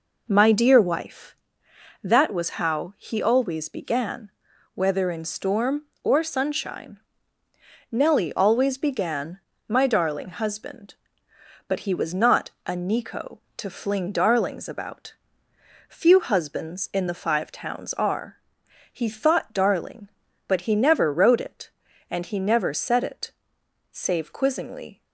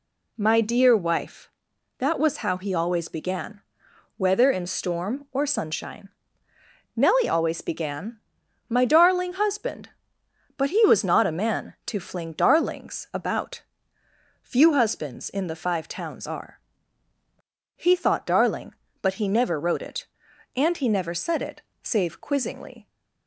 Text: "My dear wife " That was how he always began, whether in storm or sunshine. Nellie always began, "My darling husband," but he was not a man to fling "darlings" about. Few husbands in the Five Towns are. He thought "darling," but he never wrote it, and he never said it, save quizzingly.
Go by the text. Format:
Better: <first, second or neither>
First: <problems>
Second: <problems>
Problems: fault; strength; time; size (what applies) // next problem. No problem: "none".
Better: second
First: says "nico" for "man"; at 12.7 s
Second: none